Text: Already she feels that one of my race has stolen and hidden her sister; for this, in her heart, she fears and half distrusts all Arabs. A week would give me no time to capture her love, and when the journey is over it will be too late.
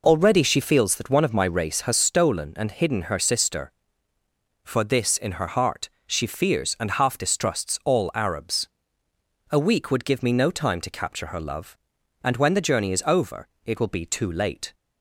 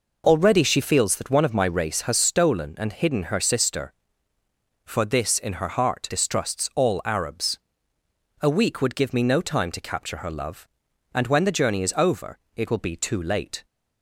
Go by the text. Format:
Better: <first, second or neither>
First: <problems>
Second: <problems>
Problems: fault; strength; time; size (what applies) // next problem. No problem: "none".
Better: first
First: pauses between "over" and "it"; slight; at 13.4 s; 0.16 s long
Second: skips "she fears and half"; at 6.0 s // pauses between "over" and "it"; slight; at 12.3 s; 0.16 s long